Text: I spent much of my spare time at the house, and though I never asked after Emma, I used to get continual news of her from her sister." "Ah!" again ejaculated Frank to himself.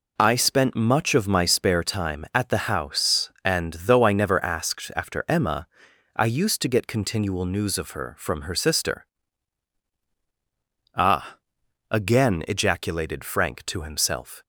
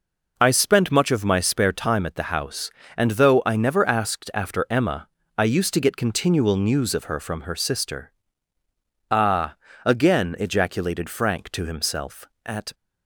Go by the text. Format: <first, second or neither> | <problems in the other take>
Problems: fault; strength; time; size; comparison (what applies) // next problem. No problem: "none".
first | goes on to say "At"; slight; from 12.4 s on; 0.30 s long